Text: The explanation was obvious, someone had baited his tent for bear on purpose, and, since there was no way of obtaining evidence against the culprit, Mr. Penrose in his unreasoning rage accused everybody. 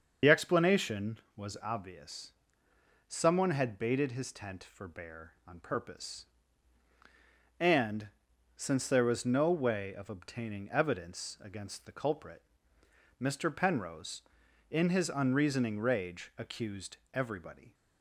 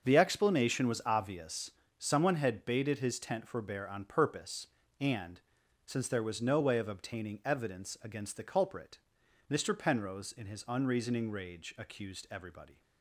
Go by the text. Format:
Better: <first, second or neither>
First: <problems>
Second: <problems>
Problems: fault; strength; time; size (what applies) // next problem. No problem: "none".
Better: second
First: loses the start of "The"; at 0.2 s; 45 ms // starts louder than the rest; until 1.4 s; 6.5 dB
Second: starts louder than the rest; until 1.0 s; 6.5 dB